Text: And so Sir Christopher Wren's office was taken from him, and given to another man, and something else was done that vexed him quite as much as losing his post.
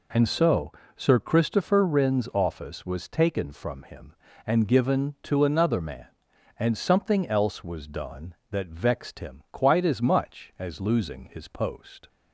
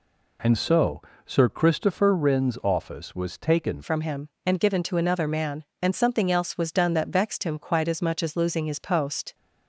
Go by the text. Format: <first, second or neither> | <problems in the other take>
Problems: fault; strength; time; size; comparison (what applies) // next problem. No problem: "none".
first | pauses between "so" and "Sir"; slight; at 1.0 s; 0.24 s long; slight in the first // changes voice at "from"; from 3.8 s on; 5.5 s long